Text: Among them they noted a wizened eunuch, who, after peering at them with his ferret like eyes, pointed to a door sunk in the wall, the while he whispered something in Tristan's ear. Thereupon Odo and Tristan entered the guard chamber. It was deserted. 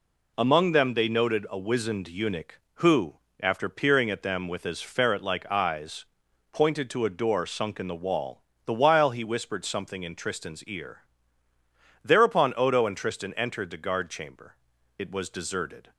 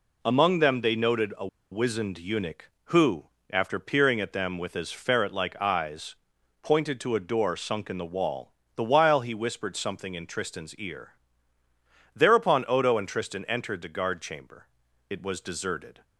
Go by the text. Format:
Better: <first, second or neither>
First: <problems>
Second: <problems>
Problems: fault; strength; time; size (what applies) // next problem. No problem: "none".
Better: first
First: none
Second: pauses between "a" and "wizened"; slight; at 1.4 s; 0.24 s long